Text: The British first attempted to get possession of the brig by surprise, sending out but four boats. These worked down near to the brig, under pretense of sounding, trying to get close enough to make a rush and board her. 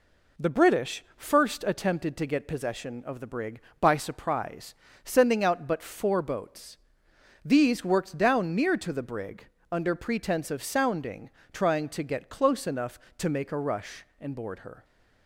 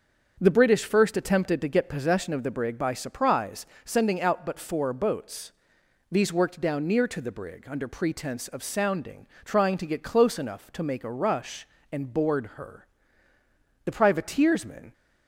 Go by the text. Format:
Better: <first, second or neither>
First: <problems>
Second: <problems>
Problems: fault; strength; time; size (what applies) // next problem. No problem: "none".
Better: first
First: none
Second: starts louder than the rest; until 1.4 s; 7 dB // goes on to say "The privateersmen"; noticeable; from 13.8 s on; 1.0 s long